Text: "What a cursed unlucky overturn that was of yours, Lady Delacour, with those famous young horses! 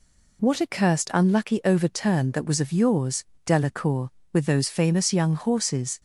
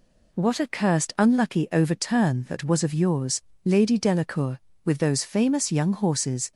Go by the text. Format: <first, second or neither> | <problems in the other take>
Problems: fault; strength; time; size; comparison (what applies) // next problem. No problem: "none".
second | skips "Lady"; at 3.3 s